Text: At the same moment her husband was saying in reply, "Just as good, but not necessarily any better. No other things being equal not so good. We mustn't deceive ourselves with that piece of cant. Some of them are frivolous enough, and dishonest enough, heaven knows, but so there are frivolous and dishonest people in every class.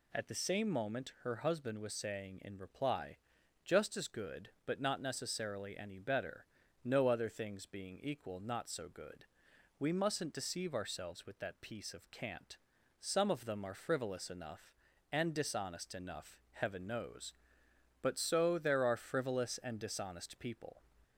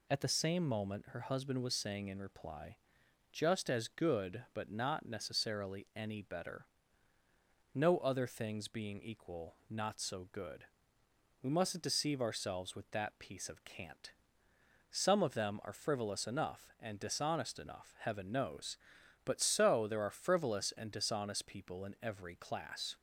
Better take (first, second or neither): second